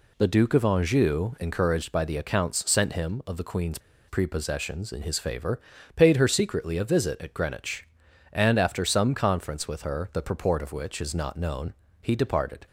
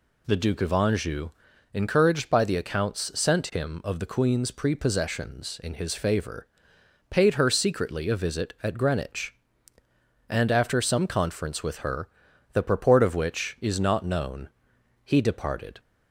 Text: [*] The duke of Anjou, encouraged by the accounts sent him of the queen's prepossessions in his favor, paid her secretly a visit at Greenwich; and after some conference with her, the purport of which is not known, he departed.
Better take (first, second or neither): second